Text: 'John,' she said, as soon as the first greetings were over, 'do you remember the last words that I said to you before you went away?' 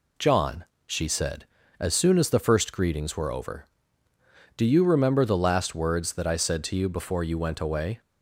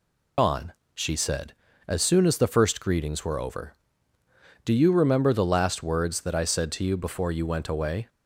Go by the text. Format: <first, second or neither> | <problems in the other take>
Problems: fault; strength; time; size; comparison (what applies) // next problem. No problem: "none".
first | loses the start of "John"; at 0.3 s; 115 ms